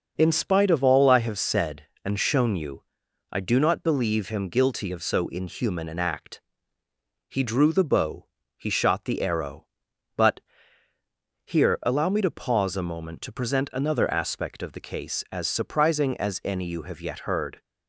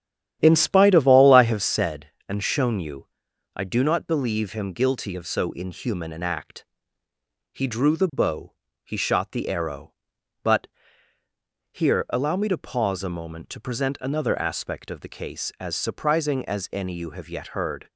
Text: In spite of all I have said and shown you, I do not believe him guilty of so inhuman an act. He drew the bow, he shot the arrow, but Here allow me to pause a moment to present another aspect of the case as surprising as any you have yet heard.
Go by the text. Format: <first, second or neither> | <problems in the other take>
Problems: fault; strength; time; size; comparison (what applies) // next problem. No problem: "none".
first | starts louder than the rest; strong; until 1.9 s; 10.5 dB // pauses between "but" and "Here"; at 10.6 s; 1.0 s long; also in the first